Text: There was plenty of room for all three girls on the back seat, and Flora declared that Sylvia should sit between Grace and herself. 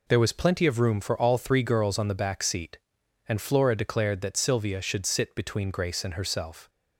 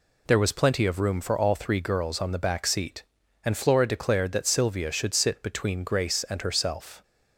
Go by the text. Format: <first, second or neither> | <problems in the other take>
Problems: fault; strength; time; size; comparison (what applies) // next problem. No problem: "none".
neither | none